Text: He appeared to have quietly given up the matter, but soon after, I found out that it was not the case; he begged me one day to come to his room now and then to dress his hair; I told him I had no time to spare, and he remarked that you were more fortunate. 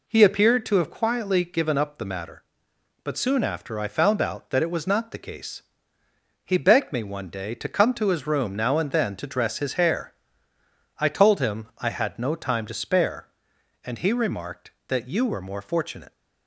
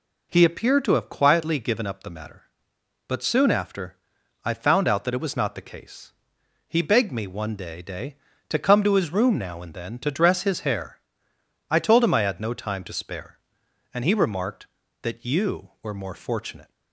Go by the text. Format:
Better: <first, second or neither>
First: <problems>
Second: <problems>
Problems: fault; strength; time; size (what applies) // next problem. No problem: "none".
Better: first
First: none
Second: says "day" twice; at 7.8 s